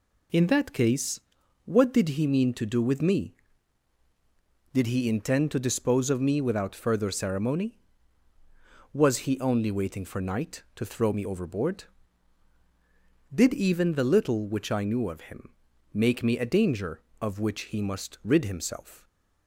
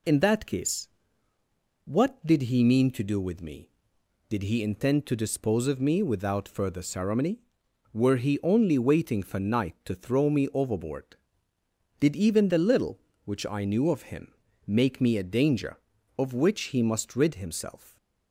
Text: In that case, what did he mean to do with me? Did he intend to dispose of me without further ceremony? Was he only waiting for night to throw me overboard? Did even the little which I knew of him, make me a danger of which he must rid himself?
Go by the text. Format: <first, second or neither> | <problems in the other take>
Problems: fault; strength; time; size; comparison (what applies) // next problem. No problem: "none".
first | says "Were" for "Was"; at 7.9 s